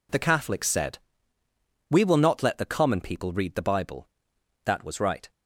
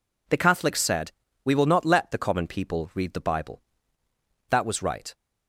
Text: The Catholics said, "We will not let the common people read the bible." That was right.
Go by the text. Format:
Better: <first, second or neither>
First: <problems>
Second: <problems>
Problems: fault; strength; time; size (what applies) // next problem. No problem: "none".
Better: neither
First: none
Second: none